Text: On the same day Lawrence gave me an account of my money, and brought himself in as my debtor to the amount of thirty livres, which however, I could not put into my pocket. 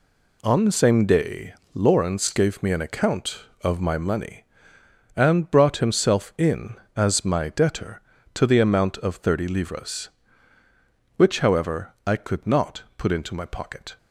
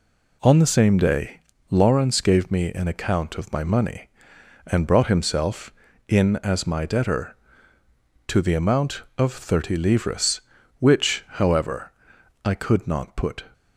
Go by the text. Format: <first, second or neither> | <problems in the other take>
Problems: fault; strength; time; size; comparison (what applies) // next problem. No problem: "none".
first | pauses between "day" and "Lawrence"; slight; at 1.4 s; 0.28 s long; slight in the first // stops before "into my pocket"; at 13.5 s